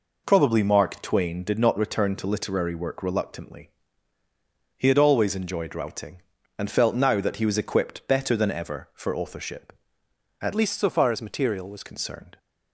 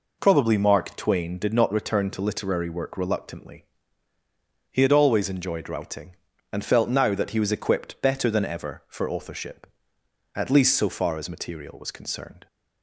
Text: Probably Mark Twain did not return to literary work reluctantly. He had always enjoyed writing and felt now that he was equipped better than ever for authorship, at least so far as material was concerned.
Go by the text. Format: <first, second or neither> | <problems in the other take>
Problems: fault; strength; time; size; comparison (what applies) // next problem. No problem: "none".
second | changes voice from "least" to "was"; from 10.5 to 11.8 s; 1.3 s long